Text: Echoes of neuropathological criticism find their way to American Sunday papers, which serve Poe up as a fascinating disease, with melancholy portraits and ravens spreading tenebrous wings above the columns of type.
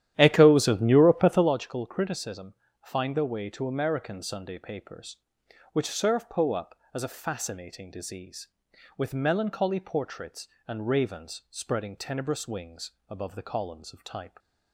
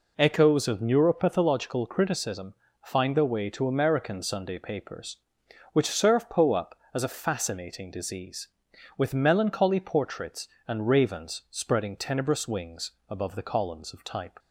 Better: second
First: starts louder than the rest; strong; until 1.6 s; 11.5 dB // pauses between "criticism" and "find"; slight; at 2.5 s; 0.32 s long // pauses between "wings" and "above"; slight; at 12.9 s; 0.16 s long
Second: pauses between "criticism" and "find"; slight; at 2.5 s; 0.32 s long // pauses between "wings" and "above"; slight; at 12.9 s; 0.16 s long

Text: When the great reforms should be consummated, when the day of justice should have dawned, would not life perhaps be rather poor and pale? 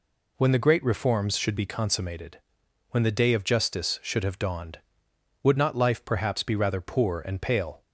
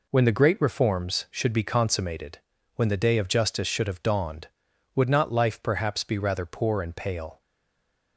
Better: first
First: none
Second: stays silent after the last word; slight; from 7.3 s on; 0.8 s long

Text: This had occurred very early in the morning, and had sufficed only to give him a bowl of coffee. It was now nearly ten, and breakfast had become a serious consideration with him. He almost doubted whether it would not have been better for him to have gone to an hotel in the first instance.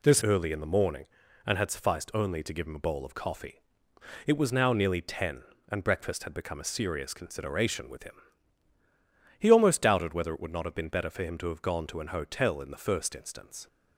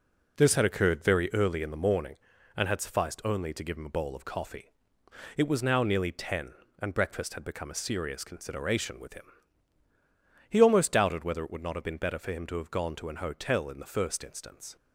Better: second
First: skips "had occurred very"; at 0.2 s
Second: none

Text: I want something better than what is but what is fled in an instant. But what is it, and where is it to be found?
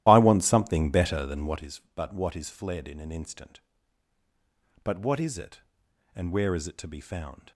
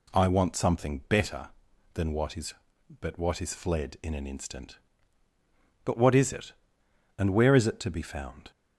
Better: second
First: starts louder than the rest; strong; until 1.7 s; 13.5 dB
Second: none

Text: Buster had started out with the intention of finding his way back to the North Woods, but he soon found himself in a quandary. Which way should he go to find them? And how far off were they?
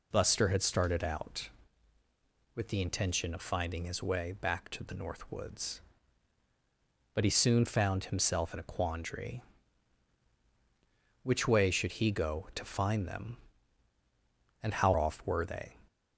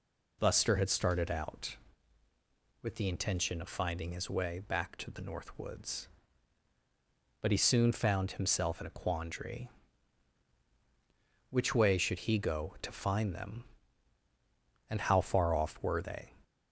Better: second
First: skips "far"; at 14.9 s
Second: none

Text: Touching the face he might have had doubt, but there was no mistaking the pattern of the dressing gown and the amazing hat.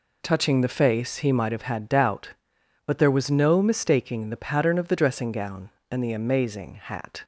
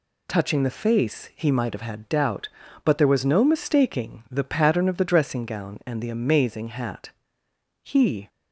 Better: first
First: none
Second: goes on to say "He"; slight; from 7.8 s on; 0.44 s long

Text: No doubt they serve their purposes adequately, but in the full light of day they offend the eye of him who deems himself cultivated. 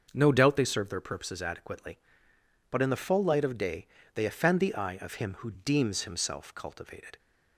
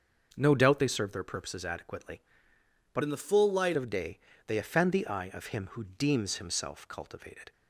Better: first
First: starts louder than the rest; until 1.1 s; 6.5 dB // pauses between "day" and "they"; slight; at 3.8 s; 0.30 s long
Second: starts louder than the rest; until 1.3 s; 6.5 dB // changes voice from "in" to "light"; from 3.0 to 3.7 s; 0.7 s long // pauses between "day" and "they"; slight; at 4.1 s; 0.30 s long

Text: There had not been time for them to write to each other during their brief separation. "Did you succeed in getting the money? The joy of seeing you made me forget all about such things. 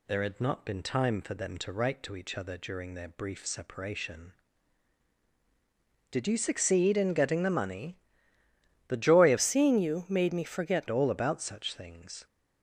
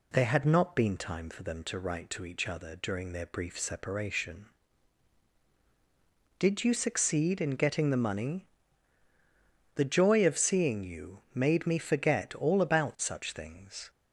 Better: second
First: changes voice from "seeing" to "forget"; from 9.3 to 10.8 s; 1.5 s long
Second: none

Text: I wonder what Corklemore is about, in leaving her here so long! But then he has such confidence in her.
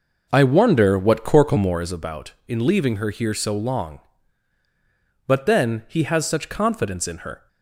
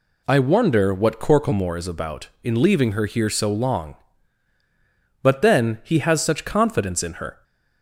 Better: second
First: starts louder than the rest; noticeable; until 2.0 s; 5.5 dB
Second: none

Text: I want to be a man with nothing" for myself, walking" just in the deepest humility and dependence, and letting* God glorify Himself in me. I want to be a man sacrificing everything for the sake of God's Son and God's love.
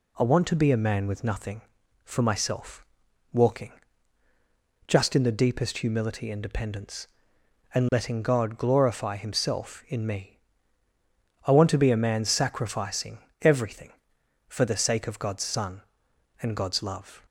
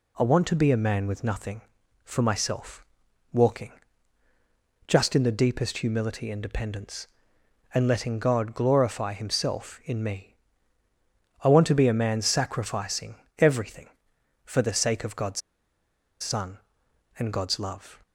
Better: first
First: pauses between "walking" and "just"; at 3.7 s; 1.1 s long // pauses between "sacrificing" and "everything"; slight; at 13.1 s; 0.22 s long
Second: pauses between "walking" and "just"; at 3.7 s; 1.1 s long // pauses between "sacrificing" and "everything"; slight; at 13.1 s; 0.22 s long // pauses between "God's" and "Son"; noticeable; at 15.3 s; 0.80 s long

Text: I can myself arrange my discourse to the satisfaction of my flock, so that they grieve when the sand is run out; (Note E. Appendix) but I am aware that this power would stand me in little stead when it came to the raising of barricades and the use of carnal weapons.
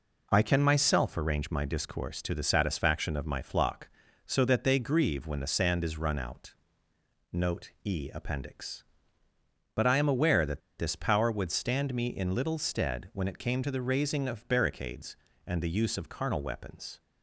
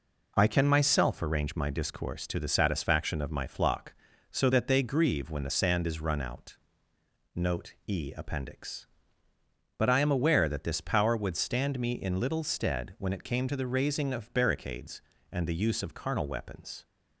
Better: second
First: pauses between "that" and "this"; slight; at 10.6 s; 0.18 s long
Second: none

